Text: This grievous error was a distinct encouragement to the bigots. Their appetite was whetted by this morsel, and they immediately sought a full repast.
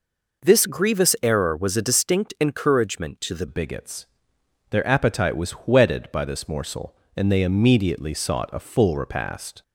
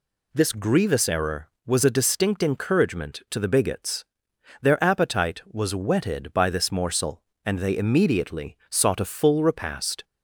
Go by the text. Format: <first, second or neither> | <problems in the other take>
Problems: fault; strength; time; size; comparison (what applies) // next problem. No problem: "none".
second | changes voice at "bigots"; from 3.4 s on; 6.2 s long